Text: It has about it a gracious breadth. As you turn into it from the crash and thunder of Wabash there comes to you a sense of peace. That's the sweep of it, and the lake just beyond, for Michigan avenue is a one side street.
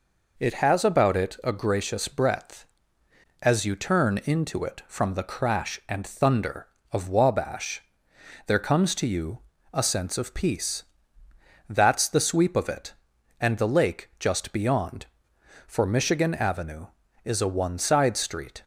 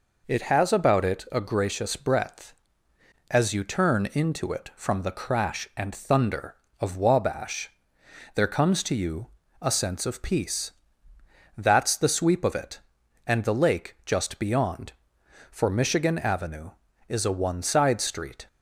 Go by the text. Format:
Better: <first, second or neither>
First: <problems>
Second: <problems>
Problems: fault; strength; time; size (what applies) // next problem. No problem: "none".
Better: neither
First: pauses between "Wabash" and "there"; noticeable; at 7.8 s; 0.66 s long // pauses between "you" and "a"; slight; at 9.3 s; 0.34 s long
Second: pauses between "Wabash" and "there"; noticeable; at 7.6 s; 0.66 s long // pauses between "you" and "a"; slight; at 9.2 s; 0.34 s long